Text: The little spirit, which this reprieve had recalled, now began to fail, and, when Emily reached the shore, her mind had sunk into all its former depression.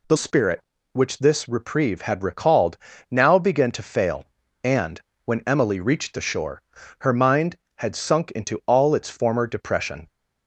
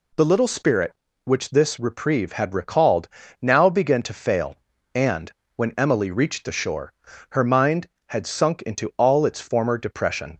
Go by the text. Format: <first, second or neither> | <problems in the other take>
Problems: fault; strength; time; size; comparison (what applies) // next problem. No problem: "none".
second | skips "little"; at 0.1 s